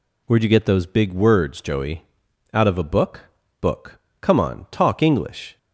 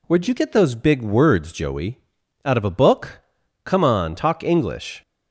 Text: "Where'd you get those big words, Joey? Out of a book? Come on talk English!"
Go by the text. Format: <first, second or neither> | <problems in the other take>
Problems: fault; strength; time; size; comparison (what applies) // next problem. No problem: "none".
second | says "book" twice; at 3.5 s